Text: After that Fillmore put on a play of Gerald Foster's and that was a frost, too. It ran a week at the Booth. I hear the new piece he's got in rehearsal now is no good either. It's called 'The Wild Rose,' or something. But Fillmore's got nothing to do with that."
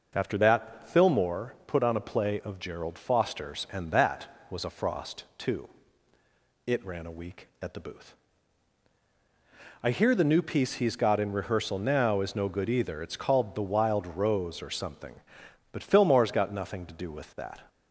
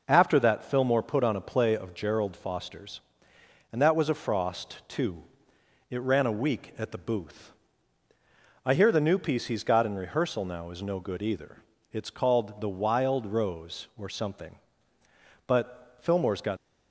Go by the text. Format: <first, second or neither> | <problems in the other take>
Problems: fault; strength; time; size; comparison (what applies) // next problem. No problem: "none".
first | stops before "nothing to do with that"; at 16.5 s